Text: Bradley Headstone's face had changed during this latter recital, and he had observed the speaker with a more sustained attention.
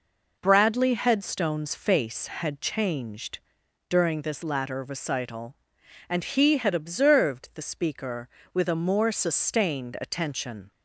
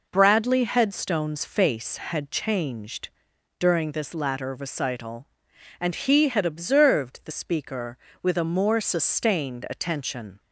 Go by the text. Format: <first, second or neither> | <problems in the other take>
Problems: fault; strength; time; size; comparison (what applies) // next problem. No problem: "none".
neither | pauses between "changed" and "during"; noticeable; the same in both